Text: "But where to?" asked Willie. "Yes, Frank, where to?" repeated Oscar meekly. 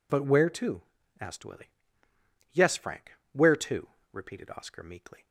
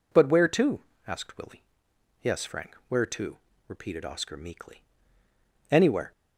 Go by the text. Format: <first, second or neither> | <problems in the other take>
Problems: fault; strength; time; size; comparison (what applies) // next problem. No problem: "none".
first | goes on to say "Anywhere"; slight; from 5.6 s on; 0.42 s long